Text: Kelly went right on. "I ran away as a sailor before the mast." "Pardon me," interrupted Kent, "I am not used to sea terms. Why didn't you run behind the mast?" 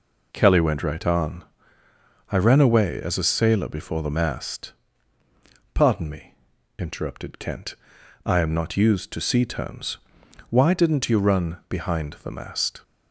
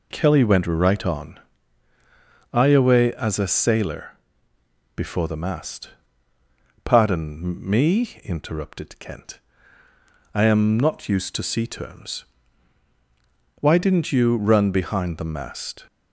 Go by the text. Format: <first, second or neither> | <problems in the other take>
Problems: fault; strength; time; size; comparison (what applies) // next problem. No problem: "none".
first | skips "ran"; at 2.6 s // pauses between "sailor" and "before"; noticeable; at 4.1 s; 0.82 s long